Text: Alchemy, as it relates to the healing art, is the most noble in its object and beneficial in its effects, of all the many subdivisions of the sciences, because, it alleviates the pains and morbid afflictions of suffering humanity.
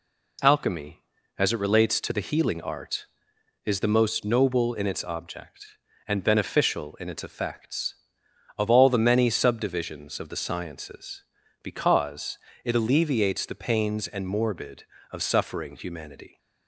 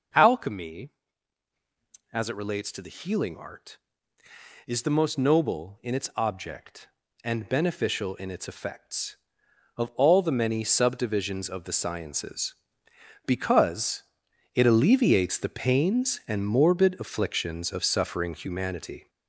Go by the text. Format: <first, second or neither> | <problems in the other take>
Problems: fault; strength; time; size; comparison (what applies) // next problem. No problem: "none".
second | skips "afflictions"; at 14.9 s